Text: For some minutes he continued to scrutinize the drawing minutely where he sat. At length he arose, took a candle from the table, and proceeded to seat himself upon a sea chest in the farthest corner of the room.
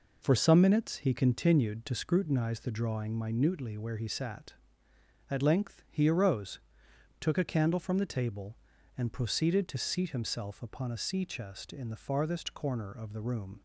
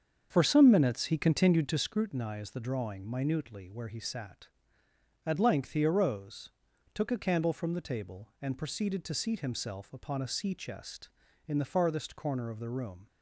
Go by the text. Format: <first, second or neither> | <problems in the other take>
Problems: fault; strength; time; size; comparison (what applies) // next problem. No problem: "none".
first | starts louder than the rest; strong; until 1.9 s; 7 dB